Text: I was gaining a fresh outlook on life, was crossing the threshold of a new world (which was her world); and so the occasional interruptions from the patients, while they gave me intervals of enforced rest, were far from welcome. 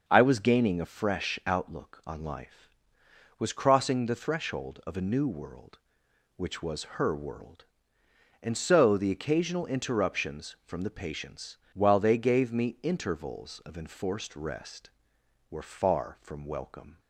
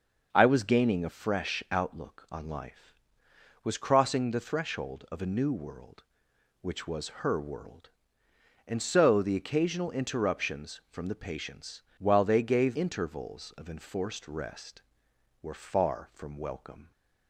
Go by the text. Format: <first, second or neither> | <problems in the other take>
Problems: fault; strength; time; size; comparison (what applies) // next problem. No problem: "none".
first | starts louder than the rest; until 1.3 s; 6 dB; also in the first // skips "me"; at 12.7 s